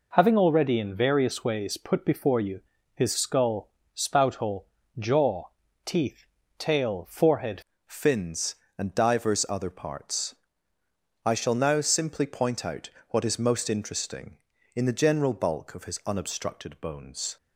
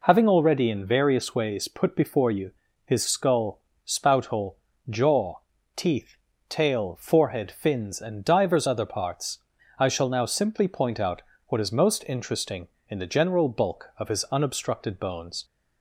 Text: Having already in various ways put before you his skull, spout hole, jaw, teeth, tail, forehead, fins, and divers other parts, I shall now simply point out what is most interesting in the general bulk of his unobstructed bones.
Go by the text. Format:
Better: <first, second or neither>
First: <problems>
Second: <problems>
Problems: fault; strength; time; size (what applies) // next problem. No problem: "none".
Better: second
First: pauses between "you" and "his"; slight; at 2.5 s; 0.34 s long // changes voice at "fins"; from 7.8 s on; 9.5 s long // pauses between "out" and "what"; slight; at 12.8 s; 0.22 s long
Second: pauses between "you" and "his"; slight; at 2.5 s; 0.34 s long // pauses between "out" and "what"; slight; at 11.2 s; 0.28 s long